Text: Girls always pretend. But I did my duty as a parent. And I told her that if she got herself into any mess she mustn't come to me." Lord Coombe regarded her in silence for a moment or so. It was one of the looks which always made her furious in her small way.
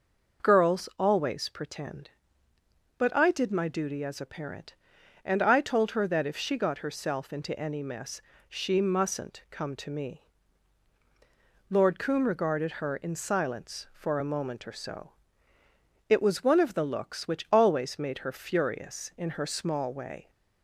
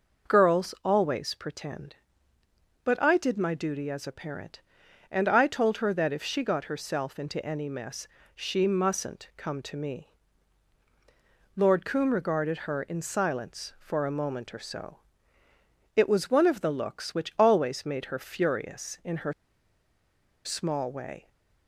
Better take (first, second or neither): first